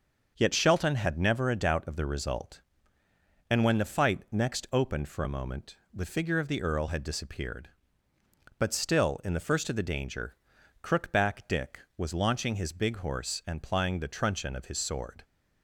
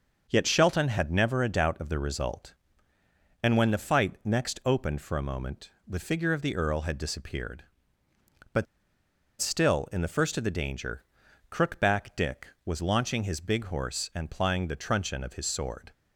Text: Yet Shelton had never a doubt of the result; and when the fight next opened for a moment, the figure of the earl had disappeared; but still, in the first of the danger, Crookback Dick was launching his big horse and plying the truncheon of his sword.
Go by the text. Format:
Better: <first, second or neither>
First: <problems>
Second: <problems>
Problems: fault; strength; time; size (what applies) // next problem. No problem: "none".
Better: first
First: starts louder than the rest; until 1.3 s; 6.5 dB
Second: starts louder than the rest; until 1.2 s; 6.5 dB // pauses between "but" and "still"; noticeable; at 8.6 s; 0.76 s long